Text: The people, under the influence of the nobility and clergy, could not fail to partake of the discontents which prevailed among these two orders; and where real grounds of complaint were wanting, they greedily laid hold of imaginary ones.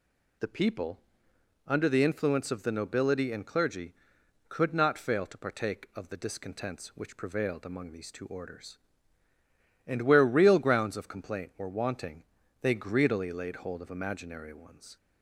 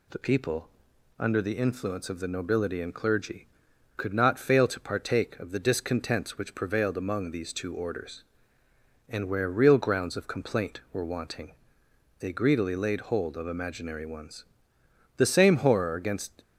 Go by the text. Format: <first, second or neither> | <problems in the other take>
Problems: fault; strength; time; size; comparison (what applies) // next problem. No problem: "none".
first | goes on to say "The same horror against"; noticeable; from 15.1 s on; 1.2 s long